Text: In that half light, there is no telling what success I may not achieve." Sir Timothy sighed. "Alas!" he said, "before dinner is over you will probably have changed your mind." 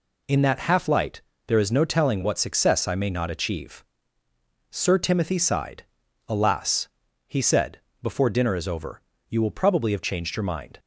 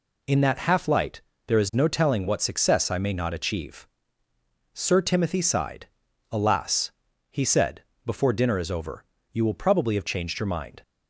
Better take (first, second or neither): neither